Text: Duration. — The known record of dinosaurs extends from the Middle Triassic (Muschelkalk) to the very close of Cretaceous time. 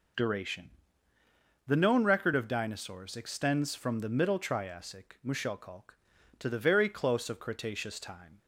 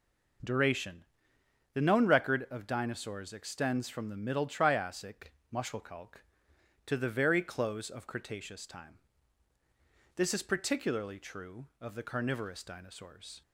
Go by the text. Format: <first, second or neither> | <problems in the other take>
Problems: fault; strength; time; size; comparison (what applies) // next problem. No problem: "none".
first | goes on to say "This is particularly true of the carnivorous dinosaurs"; strong; from 10.1 s on; 3.2 s long